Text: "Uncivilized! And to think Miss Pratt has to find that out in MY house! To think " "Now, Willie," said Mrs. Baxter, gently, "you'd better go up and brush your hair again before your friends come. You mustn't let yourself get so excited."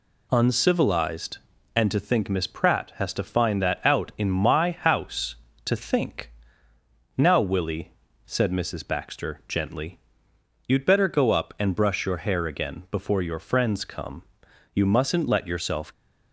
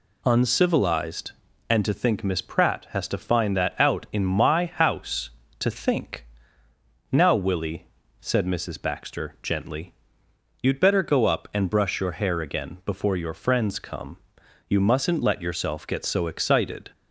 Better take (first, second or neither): second